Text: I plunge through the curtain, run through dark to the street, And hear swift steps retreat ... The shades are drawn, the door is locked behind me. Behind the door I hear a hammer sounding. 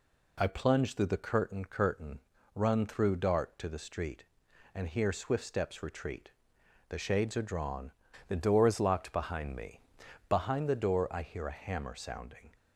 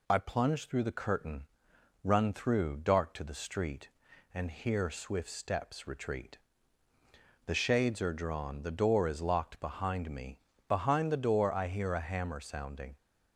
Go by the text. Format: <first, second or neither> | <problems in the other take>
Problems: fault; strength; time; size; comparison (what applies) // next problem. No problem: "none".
second | says "curtain" twice; at 1.6 s